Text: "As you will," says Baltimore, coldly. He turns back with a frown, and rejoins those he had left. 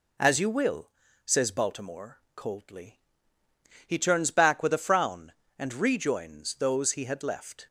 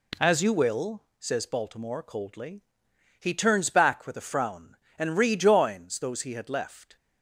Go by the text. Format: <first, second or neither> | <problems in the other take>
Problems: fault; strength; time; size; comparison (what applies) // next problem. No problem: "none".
neither | none